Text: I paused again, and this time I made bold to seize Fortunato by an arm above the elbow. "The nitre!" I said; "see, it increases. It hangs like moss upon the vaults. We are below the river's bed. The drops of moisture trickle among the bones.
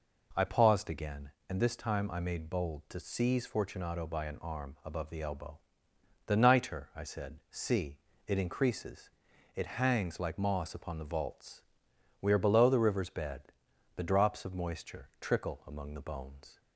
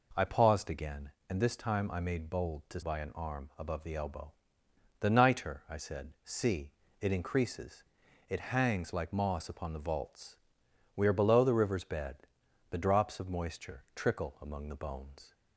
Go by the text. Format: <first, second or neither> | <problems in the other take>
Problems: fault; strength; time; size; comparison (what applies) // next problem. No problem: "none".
first | skips "seize Fortunato"; at 2.8 s